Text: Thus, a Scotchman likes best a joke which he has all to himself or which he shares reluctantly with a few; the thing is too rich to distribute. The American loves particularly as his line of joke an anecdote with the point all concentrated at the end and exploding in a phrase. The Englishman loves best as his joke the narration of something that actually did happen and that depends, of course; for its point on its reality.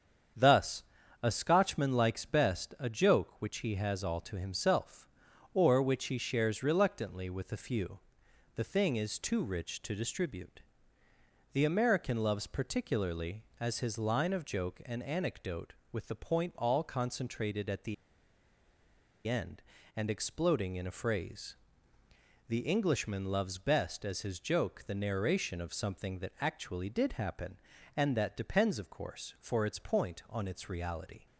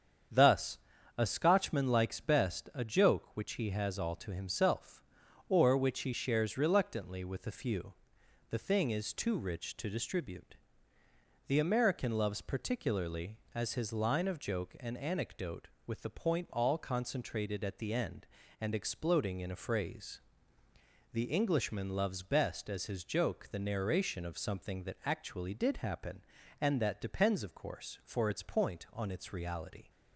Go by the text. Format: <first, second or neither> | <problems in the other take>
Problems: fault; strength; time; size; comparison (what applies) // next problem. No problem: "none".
second | starts louder than the rest; strong; until 1.7 s; 7.5 dB; strong in the second // pauses between "the" and "end"; strong; at 17.9 s; 1.3 s long